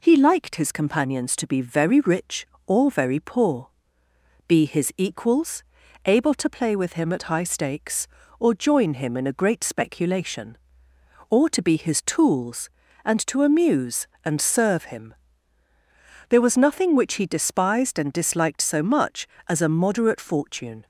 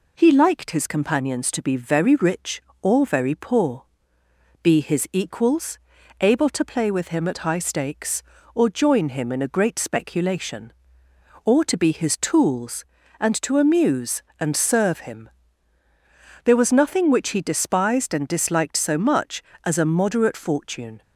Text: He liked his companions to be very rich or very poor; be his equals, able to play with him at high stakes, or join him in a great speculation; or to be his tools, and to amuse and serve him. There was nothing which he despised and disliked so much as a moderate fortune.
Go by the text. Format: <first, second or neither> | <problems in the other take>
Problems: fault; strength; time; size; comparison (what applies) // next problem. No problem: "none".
neither | none